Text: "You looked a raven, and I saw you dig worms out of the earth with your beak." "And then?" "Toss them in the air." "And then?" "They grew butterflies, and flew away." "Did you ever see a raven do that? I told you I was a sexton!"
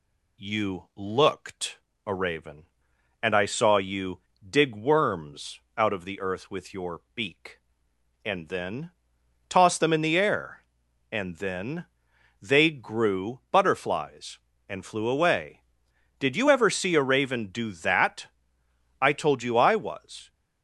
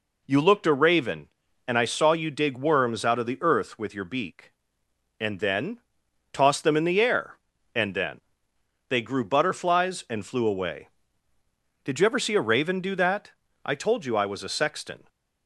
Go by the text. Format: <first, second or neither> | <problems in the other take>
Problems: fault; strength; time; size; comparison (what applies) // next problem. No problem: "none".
second | pauses between "looked" and "a"; slight; at 1.8 s; 0.26 s long // pauses between "you" and "dig"; slight; at 4.2 s; 0.28 s long // pauses between "worms" and "out"; slight; at 5.5 s; 0.18 s long // pauses between "your" and "beak"; slight; at 7.0 s; 0.16 s long // stops before "a sexton"; at 20.2 s